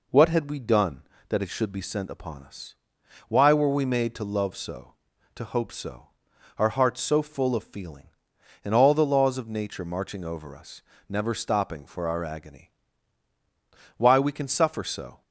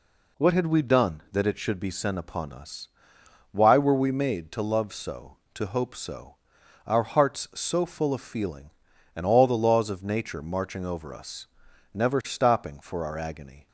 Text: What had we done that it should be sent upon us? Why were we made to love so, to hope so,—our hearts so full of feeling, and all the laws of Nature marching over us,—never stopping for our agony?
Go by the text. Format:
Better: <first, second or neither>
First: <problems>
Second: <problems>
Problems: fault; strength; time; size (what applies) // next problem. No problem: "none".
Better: second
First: goes on to say "Why we can suffer so"; noticeable; from 13.9 s on; 1.2 s long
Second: none